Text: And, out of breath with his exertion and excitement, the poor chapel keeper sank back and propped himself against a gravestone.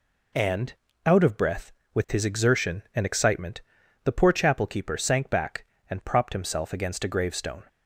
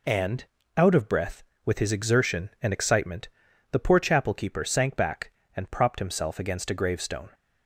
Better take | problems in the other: neither | none

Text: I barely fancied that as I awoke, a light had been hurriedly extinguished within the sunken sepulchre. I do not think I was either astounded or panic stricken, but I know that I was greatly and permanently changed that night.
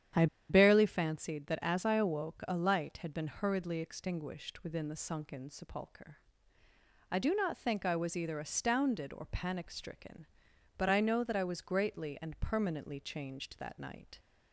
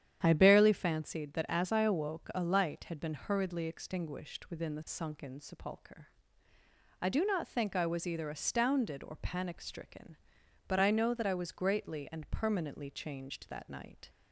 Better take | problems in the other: second | starts louder than the rest; strong; until 1.3 s; 9.5 dB; strong in the second // pauses between "I" and "barely"; slight; at 0.2 s; 0.23 s long

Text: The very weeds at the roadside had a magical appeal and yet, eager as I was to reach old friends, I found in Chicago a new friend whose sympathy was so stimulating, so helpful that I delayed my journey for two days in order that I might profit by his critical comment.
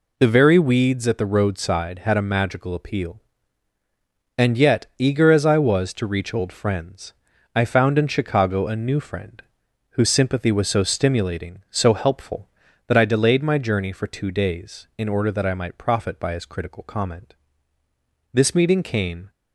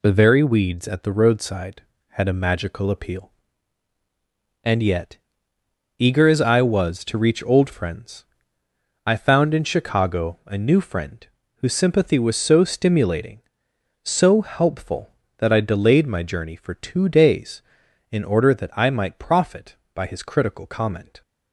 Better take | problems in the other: second | pauses between "friend" and "whose"; noticeable; at 9.4 s; 0.50 s long; slight in the second // goes on to say "This meeting came"; noticeable; from 18.3 s on; 0.98 s long

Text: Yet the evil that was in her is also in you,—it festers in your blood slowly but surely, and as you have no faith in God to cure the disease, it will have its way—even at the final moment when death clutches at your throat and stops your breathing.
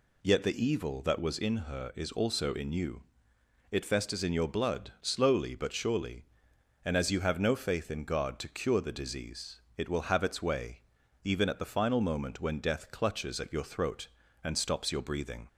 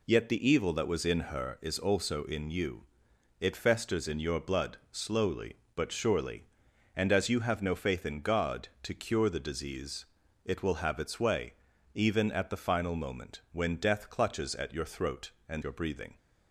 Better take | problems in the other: first | skips "stops"; at 15.6 s

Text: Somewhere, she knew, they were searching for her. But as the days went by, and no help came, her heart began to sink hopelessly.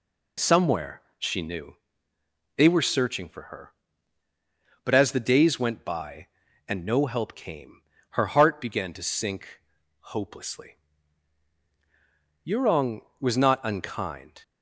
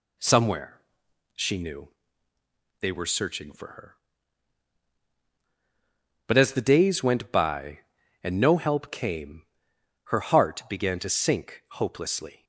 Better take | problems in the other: second | pauses between "sink" and "hopelessly"; at 9.5 s; 0.40 s long // goes on to say "Yurong was not unkind"; strong; from 12.4 s on; 1.9 s long

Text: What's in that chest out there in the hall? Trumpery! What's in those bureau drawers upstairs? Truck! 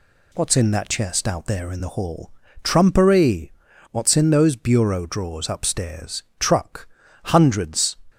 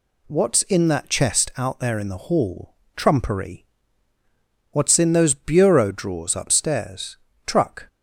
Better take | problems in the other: second | goes on to say "Hundreds"; noticeable; from 7.2 s on; 0.72 s long

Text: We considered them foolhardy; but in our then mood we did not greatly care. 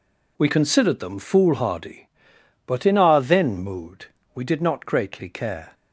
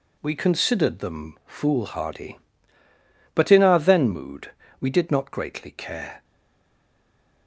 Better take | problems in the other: first | pauses between "mood" and "we"; slight; at 4.5 s; 0.28 s long; slight in the first // stays silent after the last word; noticeable; from 6.2 s on; 1.2 s long

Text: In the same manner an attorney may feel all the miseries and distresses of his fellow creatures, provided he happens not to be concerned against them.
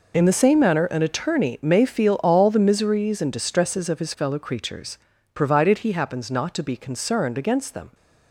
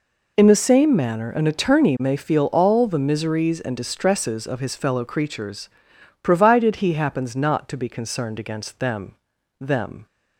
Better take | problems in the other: first | says "them" twice; at 9.5 s

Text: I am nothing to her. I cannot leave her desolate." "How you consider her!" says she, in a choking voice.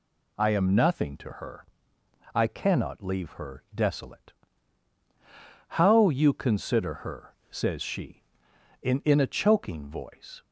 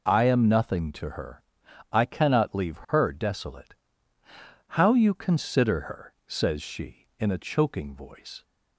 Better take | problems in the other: second | says "in" twice; at 9.0 s

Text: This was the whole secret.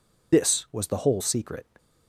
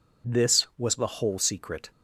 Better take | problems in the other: second | loses the start of "This"; at 0.3 s; 50 ms

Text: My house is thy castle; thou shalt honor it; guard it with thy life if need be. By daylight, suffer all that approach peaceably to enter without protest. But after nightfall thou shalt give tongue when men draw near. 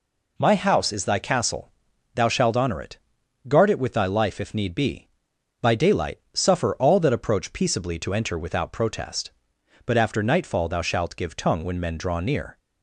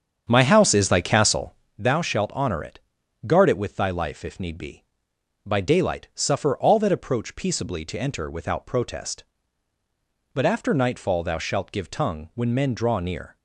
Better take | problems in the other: first | starts louder than the rest; strong; until 1.7 s; 8 dB

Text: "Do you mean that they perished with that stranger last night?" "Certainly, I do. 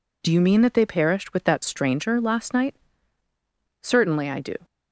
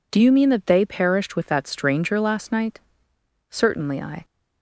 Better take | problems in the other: first | stops before "do"; at 4.2 s

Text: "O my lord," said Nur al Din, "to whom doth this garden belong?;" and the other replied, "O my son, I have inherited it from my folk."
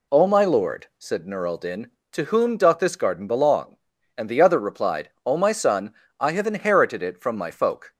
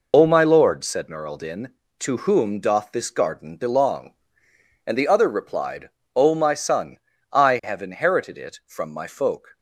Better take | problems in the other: first | loses the start of "O"; at 0.1 s; 75 ms

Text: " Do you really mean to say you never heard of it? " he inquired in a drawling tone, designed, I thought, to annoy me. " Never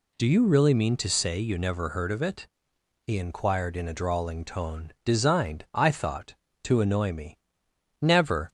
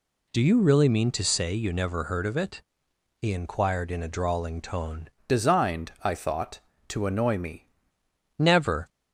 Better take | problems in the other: first | changes voice from "designed" to "me"; from 5.2 to 7.6 s; 2.4 s long

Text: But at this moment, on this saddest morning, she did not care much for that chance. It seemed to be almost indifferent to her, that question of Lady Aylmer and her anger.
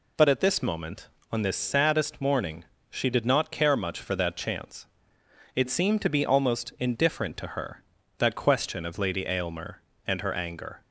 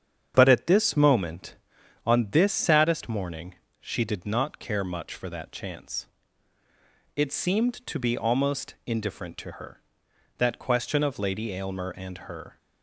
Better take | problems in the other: first | starts louder than the rest; strong; until 1.3 s; 8.5 dB // stops before "anger"; at 12.5 s

